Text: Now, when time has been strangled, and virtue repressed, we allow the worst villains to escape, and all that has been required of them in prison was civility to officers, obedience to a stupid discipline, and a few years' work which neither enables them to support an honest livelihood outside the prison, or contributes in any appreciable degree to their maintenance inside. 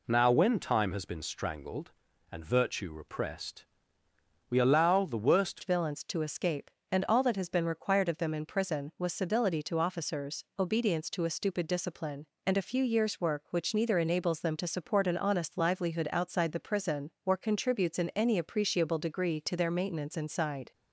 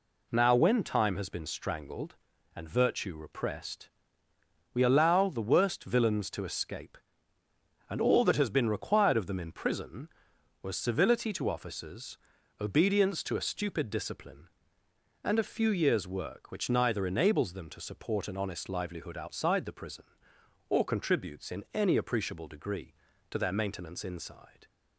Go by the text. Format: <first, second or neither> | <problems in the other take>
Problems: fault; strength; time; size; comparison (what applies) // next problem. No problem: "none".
second | changes voice at "villains"; from 5.6 s on; 15.1 s long